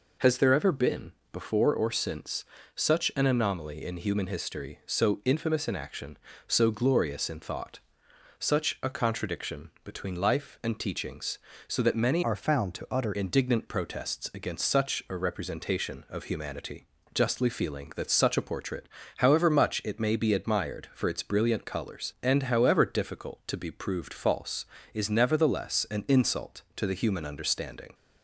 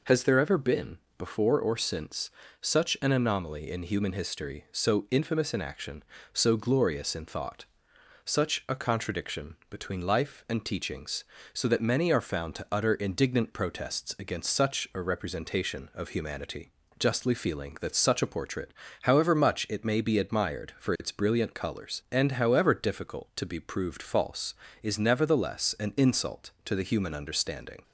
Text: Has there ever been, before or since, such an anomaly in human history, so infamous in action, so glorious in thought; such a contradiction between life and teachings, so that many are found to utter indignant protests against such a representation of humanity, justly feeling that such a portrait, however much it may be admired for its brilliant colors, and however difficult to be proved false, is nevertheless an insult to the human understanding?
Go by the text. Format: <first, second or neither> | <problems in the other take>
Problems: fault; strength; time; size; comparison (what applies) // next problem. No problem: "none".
second | changes voice from "are" to "utter"; from 12.2 to 13.1 s; 0.9 s long